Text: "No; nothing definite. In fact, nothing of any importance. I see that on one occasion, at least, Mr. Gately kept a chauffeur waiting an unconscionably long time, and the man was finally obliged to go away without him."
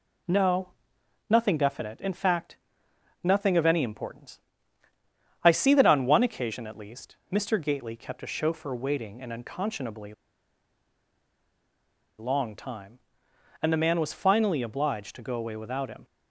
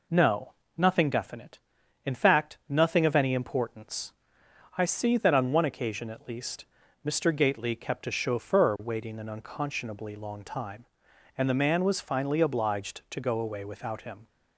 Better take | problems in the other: second | pauses between "unconscionably" and "long"; strong; at 10.1 s; 2.0 s long

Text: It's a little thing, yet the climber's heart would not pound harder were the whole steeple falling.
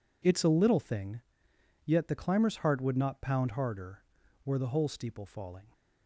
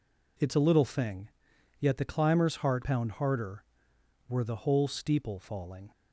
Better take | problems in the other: first | skips "would not"; at 2.8 s

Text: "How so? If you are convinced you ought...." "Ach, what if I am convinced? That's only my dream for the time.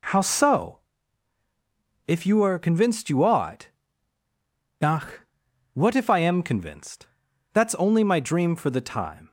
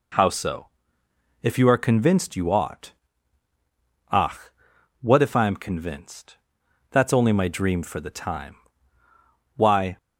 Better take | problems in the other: first | goes on to say "Why"; slight; from 9.5 s on; 0.40 s long

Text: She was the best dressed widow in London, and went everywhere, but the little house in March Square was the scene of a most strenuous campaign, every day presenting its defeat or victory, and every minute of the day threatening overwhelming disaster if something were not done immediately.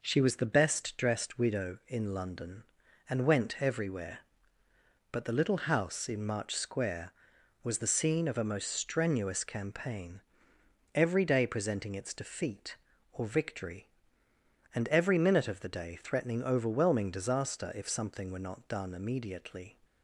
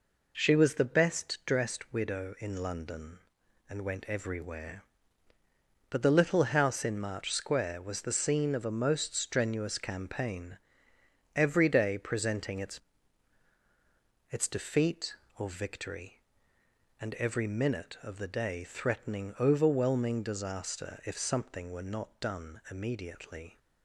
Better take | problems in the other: first | says "its" twice; at 14.2 s

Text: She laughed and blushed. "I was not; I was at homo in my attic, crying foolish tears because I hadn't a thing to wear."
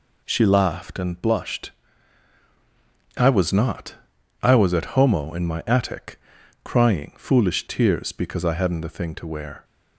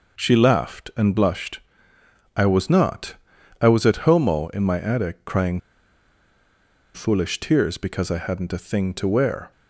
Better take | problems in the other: first | pauses between "crying" and "foolish"; strong; at 5.5 s; 1.3 s long

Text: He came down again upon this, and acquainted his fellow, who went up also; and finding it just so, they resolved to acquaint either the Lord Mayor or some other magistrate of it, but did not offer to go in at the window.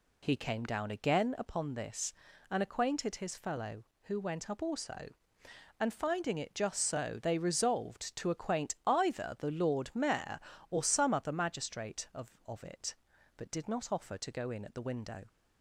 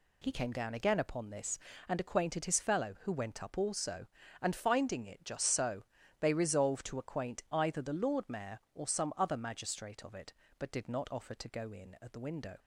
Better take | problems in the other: second | says "of" twice; at 12.4 s

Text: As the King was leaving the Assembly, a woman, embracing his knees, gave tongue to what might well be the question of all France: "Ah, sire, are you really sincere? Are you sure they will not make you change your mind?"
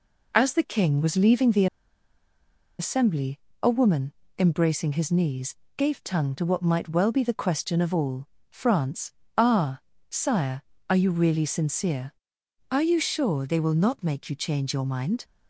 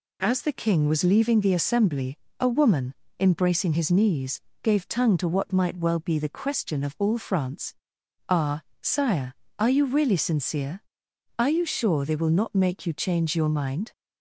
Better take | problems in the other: second | pauses between "the" and "Assembly"; at 1.6 s; 1.1 s long // pauses between "all" and "France"; slight; at 8.2 s; 0.24 s long

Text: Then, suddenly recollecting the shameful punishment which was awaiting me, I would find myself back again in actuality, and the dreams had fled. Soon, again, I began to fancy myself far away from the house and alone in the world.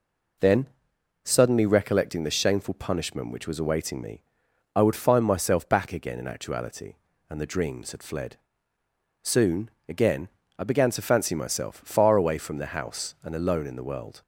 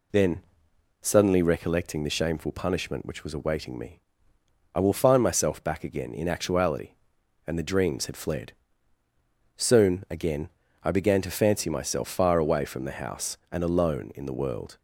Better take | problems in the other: first | says "will" for "would"; at 4.8 s

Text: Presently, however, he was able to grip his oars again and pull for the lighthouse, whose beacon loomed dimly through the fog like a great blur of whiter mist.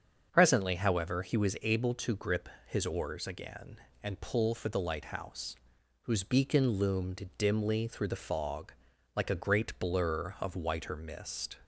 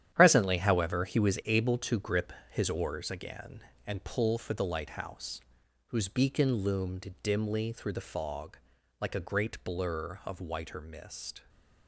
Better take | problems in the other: first | gets quieter; strong; throughout; 9 dB // starts louder than the rest; strong; until 1.1 s; 10.5 dB; also in the first // pauses between "grip" and "his"; slight; at 2.3 s; 0.18 s long; slight in the first // pauses between "fog" and "like"; at 8.5 s; 0.44 s long; also in the first

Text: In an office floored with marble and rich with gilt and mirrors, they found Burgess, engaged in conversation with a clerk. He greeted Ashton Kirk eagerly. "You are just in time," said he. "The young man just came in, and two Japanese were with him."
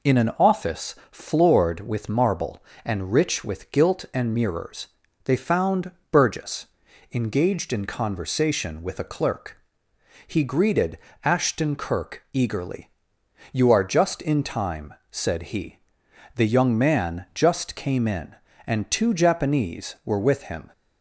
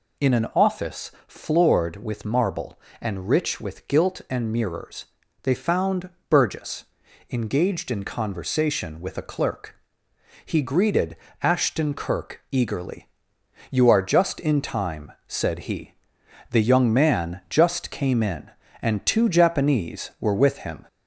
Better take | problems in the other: first | gets louder; slight; throughout; 2 dB // pauses between "office" and "floored"; slight; at 1.1 s; 0.16 s long; slight in the first // pauses between "found" and "Burgess"; slight; at 6.0 s; 0.22 s long; slight in the first // pauses between "greeted" and "Ashton"; slight; at 11.1 s; 0.26 s long; slight in the first

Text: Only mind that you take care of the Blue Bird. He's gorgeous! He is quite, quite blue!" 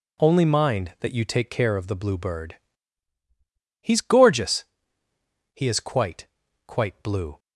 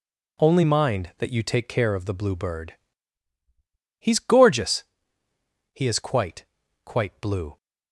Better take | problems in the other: neither | none

